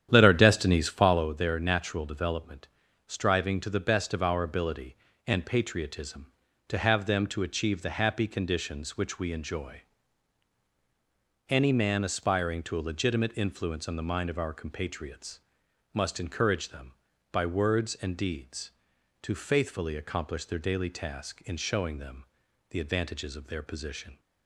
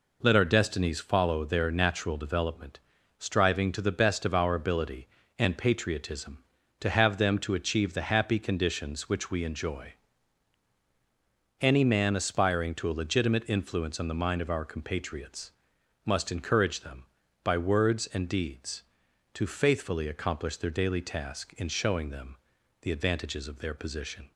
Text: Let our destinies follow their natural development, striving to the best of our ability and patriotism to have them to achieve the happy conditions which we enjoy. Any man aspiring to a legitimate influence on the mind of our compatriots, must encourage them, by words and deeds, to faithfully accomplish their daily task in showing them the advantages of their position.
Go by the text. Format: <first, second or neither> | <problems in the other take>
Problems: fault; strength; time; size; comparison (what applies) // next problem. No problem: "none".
second | starts louder than the rest; strong; until 1.3 s; 10 dB // pauses between "them" and "the"; noticeable; at 22.2 s; 0.46 s long; noticeable in the second